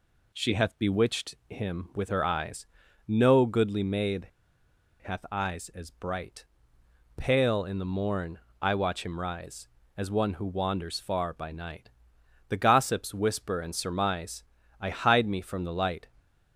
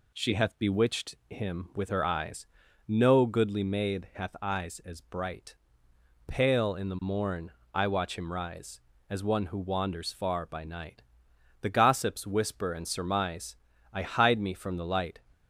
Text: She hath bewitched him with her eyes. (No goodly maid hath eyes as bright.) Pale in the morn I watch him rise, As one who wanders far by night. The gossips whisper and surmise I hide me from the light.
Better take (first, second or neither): second